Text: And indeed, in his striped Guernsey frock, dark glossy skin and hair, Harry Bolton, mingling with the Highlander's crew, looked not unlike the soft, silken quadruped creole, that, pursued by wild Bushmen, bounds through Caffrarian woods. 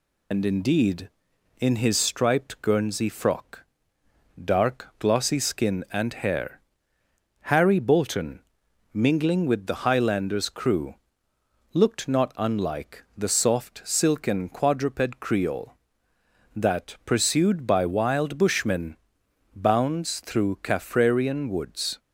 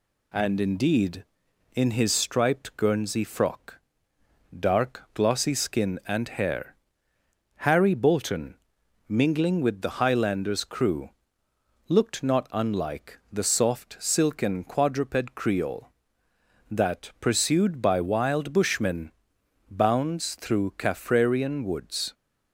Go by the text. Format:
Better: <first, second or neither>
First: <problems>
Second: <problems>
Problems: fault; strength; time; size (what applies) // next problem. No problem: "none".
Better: second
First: loses the start of "And"; at 0.3 s; 120 ms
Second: none